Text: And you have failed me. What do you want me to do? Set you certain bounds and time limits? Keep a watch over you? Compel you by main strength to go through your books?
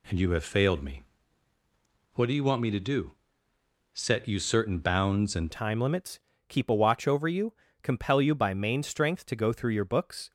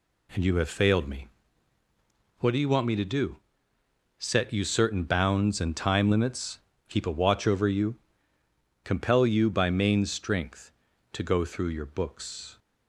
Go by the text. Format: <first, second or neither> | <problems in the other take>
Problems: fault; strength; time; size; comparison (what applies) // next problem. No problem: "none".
second | changes voice at "time"; from 5.5 s on; 4.8 s long